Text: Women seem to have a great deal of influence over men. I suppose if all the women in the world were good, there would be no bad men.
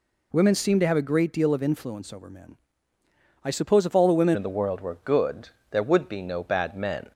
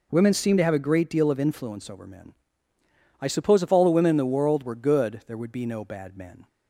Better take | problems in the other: second | changes voice at "in"; from 4.3 s on; 2.8 s long

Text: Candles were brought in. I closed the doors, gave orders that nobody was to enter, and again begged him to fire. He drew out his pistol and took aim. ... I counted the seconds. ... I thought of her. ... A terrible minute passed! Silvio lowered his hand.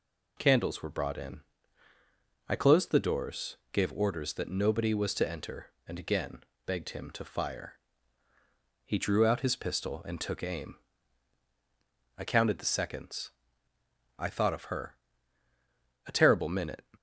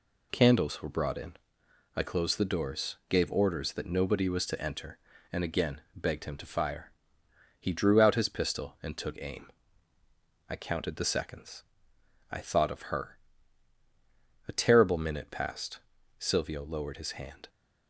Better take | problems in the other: second | pauses between "again" and "begged"; slight; at 6.4 s; 0.24 s long; slight in the second // stops before "passed Silvio lowered his hand"; at 16.9 s

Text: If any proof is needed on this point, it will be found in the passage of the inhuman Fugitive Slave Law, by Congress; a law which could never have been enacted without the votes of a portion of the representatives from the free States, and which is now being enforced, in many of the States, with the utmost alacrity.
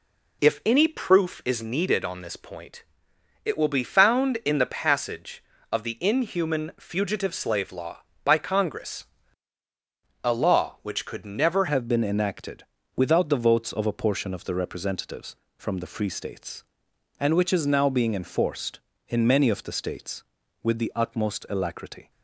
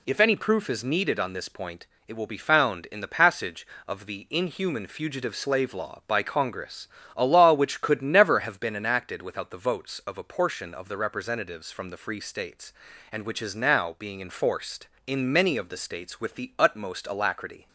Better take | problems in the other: second | changes voice at "have"; from 11.6 s on; 10.5 s long // pauses between "enacted" and "without"; slight; at 12.6 s; 0.32 s long

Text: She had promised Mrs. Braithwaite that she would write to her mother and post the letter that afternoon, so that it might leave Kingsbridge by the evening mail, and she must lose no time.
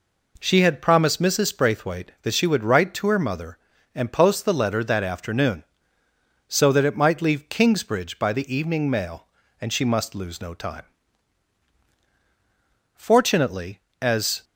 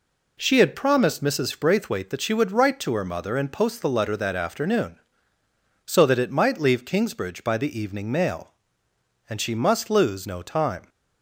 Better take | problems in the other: second | goes on to say "Fortunately as"; from 12.9 s on; 1.4 s long

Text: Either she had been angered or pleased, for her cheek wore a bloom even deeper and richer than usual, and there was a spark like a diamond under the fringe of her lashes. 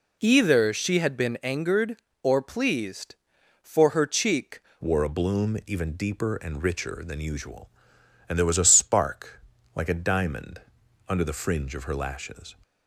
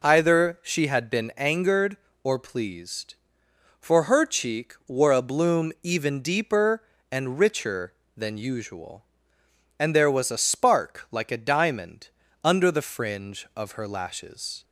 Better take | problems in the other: second | changes voice at "wore"; from 4.8 s on; 7.7 s long // pauses between "spark" and "like"; slight; at 9.4 s; 0.34 s long // pauses between "diamond" and "under"; noticeable; at 10.6 s; 0.48 s long; slight in the second

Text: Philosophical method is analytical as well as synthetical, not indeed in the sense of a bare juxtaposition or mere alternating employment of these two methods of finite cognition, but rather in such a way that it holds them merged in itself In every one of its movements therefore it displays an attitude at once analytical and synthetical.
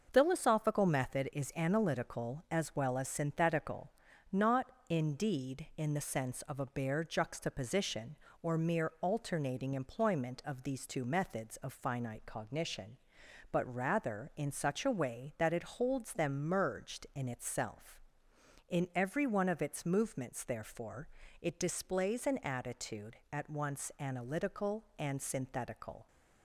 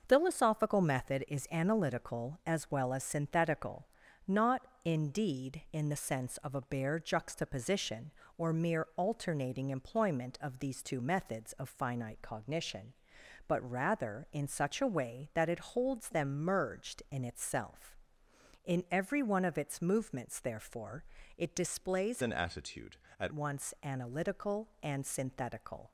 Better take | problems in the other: first | starts louder than the rest; noticeable; until 1.0 s; 6 dB; noticeable in the first // pauses between "not" and "indeed"; slight; at 4.6 s; 0.24 s long; slight in the first // pauses between "therefore" and "it"; slight; at 21.0 s; 0.36 s long; slight in the first // changes voice from "an" to "at"; from 22.2 to 23.3 s; 1.1 s long

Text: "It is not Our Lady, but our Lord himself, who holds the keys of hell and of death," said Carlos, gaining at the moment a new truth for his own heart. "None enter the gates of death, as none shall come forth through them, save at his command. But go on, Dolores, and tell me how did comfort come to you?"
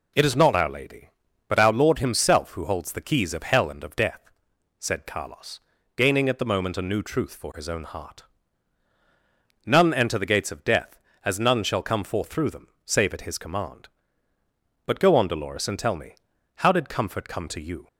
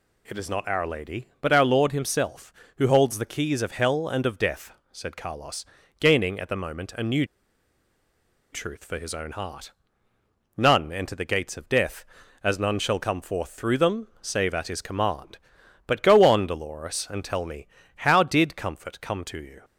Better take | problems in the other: first | pauses between "new" and "truth"; strong; at 7.2 s; 1.2 s long // pauses between "me" and "how"; slight; at 17.6 s; 0.30 s long; also in the first

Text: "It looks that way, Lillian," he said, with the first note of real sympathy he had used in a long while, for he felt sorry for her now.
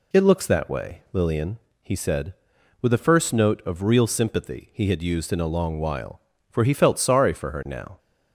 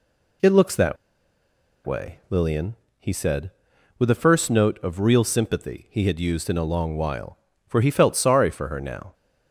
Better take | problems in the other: first | pauses between "that" and "way"; noticeable; at 0.9 s; 0.88 s long

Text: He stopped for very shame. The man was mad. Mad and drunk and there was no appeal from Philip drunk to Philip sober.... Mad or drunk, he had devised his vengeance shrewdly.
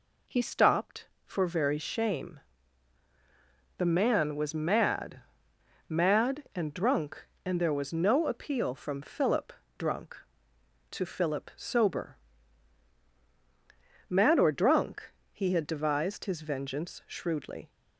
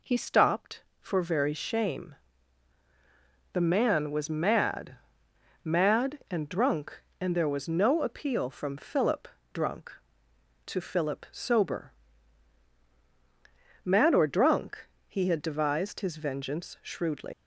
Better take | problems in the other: first | pauses between "Philip" and "drunk"; slight; at 9.2 s; 0.24 s long; slight in the first // leaves "shrewdly" unfinished; at 17.3 s; 115 ms

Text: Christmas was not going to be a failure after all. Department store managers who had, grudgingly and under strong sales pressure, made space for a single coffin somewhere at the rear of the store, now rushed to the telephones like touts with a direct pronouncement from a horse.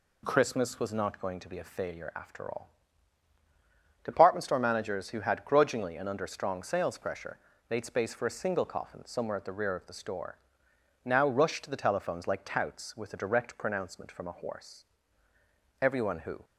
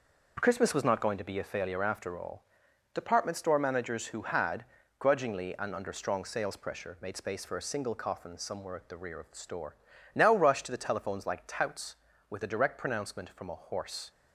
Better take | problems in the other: second | goes on to say "Everyone who"; noticeable; from 15.8 s on; 0.64 s long

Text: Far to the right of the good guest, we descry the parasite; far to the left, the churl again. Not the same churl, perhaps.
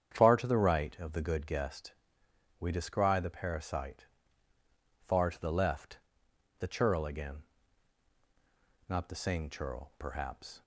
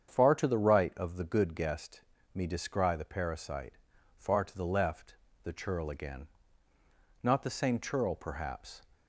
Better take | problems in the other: first | starts louder than the rest; strong; until 1.1 s; 7.5 dB; strong in the first // says "me" for "we"; at 2.3 s

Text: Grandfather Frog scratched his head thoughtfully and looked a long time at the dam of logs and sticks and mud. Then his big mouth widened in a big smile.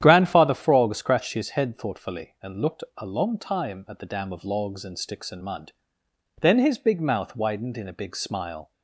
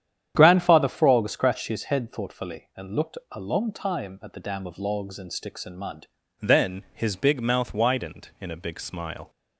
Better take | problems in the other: first | starts louder than the rest; strong; until 1.3 s; 9.5 dB; strong in the first // pauses between "looked" and "a"; slight; at 3.1 s; 0.16 s long; slight in the first // changes voice at "Then"; from 6.4 s on; 2.8 s long

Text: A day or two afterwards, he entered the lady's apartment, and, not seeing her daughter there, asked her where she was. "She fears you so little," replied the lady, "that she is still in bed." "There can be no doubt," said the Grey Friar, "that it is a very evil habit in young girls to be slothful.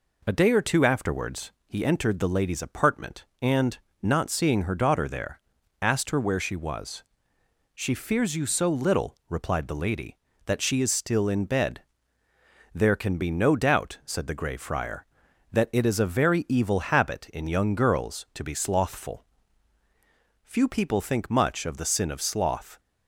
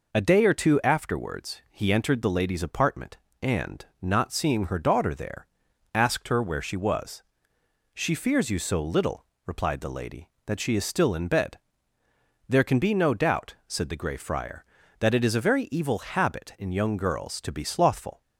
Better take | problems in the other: second | goes on to say "Few people think much of the sin of sloth"; strong; from 20.4 s on; 2.3 s long

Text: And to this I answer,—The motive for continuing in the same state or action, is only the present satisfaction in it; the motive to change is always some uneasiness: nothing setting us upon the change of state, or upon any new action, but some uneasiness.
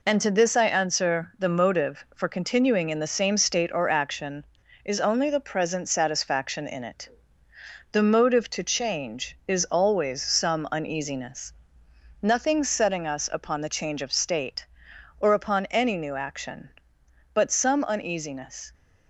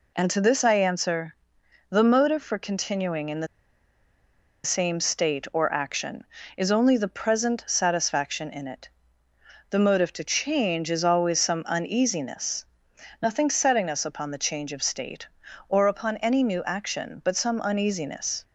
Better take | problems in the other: first | pauses between "the" and "same"; at 3.4 s; 1.1 s long

